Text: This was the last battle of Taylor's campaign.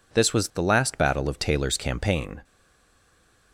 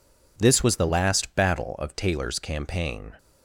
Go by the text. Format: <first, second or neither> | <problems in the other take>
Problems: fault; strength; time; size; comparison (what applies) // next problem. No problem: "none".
second | stays silent after the last word; from 2.4 s on; 1.1 s long